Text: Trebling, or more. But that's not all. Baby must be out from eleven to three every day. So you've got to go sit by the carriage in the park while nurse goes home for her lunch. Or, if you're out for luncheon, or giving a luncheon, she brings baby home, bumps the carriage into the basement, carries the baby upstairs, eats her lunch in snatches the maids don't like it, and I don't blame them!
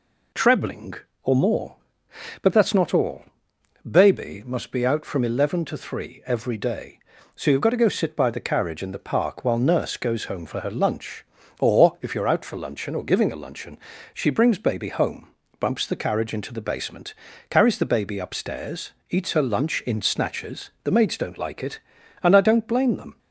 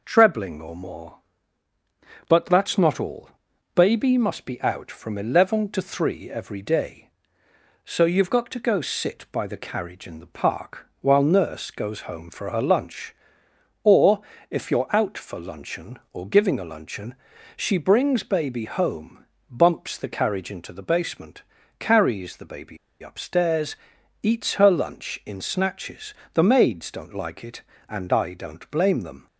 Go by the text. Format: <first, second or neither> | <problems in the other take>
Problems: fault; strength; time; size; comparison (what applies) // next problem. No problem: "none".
first | pauses between "baby" and "upstairs"; slight; at 22.7 s; 0.25 s long // pauses between "snatches" and "the"; slight; at 26.1 s; 0.20 s long